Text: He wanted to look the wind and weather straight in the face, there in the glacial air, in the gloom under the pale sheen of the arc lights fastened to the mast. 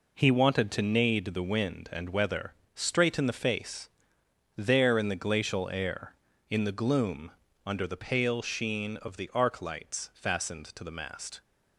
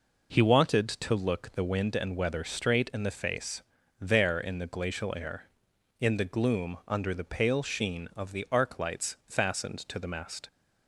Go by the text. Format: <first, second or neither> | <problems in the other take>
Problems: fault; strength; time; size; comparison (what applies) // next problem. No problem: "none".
second | says "nade" for "look"; at 0.8 s // pauses between "weather" and "straight"; slight; at 2.5 s; 0.20 s long // pauses between "gloom" and "under"; slight; at 7.3 s; 0.36 s long